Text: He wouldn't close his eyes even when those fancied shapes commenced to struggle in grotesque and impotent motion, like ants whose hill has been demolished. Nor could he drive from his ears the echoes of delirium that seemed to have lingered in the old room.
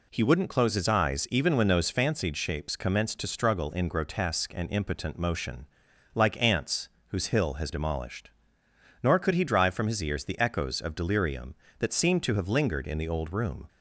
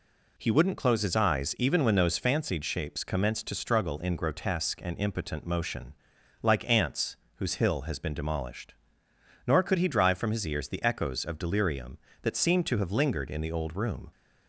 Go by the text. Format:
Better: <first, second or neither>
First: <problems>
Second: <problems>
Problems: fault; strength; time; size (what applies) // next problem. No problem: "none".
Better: second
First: pauses between "ants" and "whose"; slight; at 6.8 s; 0.20 s long // skips "been"; at 7.7 s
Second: pauses between "ants" and "whose"; slight; at 7.1 s; 0.20 s long